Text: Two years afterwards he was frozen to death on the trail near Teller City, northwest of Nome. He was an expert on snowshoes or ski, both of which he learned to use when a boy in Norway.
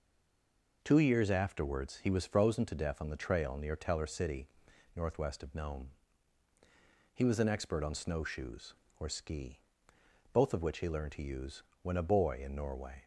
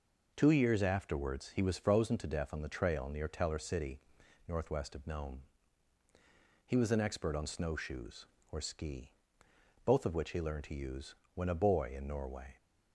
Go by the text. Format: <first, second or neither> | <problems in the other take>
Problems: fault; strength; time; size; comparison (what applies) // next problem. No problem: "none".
second | stays silent before the first word; slight; until 0.8 s; 0.8 s long // pauses between "use" and "when"; slight; at 11.6 s; 0.20 s long; slight in the second